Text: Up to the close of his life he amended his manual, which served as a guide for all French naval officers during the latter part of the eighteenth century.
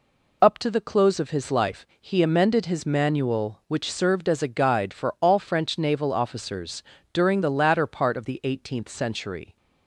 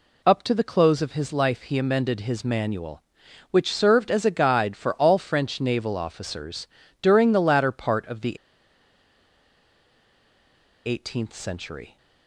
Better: first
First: pauses between "officers" and "during"; slight; at 6.8 s; 0.30 s long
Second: pauses between "officers" and "during"; slight; at 6.6 s; 0.32 s long // pauses between "the" and "eighteenth"; strong; at 8.3 s; 2.4 s long

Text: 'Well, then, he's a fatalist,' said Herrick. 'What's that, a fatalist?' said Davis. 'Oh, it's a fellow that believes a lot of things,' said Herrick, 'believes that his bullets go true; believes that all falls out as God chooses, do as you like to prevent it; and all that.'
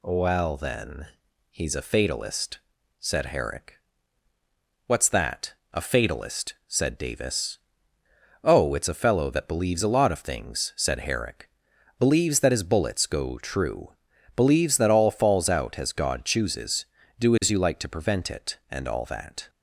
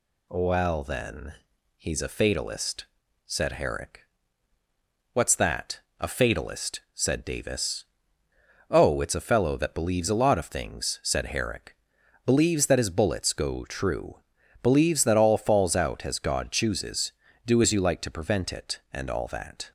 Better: neither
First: none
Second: none

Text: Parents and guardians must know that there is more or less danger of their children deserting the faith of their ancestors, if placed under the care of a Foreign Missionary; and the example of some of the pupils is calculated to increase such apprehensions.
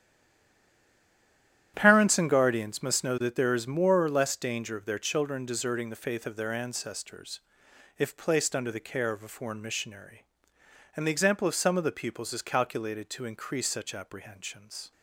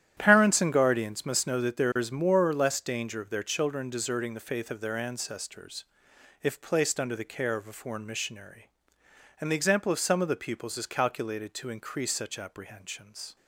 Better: second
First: stays silent before the first word; noticeable; until 1.7 s; 1.7 s long // starts louder than the rest; strong; until 2.7 s; 11 dB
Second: starts louder than the rest; strong; until 1.1 s; 11 dB

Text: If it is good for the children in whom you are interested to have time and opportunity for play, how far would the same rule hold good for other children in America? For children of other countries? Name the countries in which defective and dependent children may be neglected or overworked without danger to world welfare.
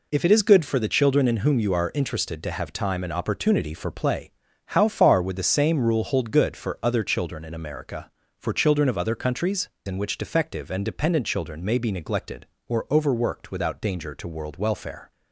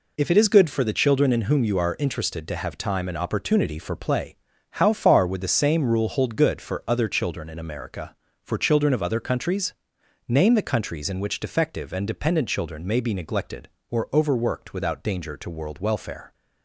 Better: second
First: skips "Name the countries"; at 9.7 s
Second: none

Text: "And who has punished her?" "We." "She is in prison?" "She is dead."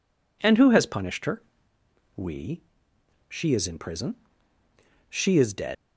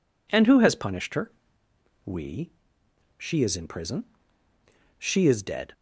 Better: second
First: leaves "dead" unfinished; at 5.7 s; 85 ms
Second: none

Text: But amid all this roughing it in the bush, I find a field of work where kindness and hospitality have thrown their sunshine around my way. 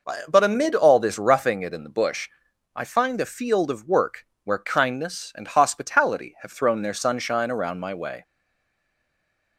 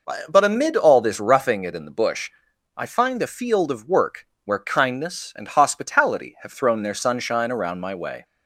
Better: second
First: pauses between "work" and "where"; slight; at 4.2 s; 0.20 s long // stays silent after the last word; noticeable; from 8.2 s on; 1.3 s long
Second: pauses between "work" and "where"; slight; at 4.2 s; 0.20 s long

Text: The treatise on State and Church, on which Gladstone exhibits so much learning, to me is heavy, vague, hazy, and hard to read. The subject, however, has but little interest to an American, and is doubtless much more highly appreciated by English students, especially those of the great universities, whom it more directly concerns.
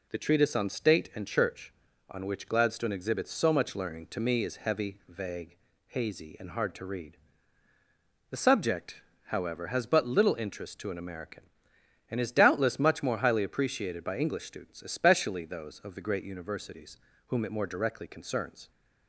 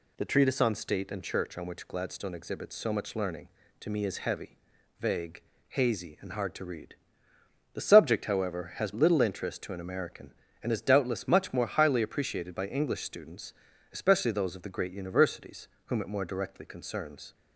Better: first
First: none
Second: skips "but"; at 8.9 s

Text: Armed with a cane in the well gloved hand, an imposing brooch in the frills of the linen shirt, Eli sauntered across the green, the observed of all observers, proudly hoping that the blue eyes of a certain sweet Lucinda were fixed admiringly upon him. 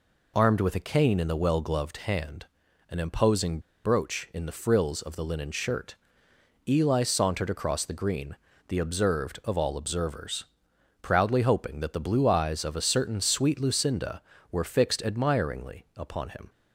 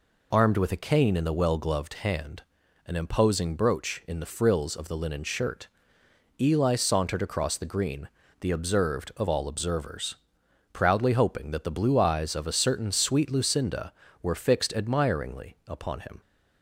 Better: second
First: pauses between "imposing" and "brooch"; slight; at 3.5 s; 0.25 s long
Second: none

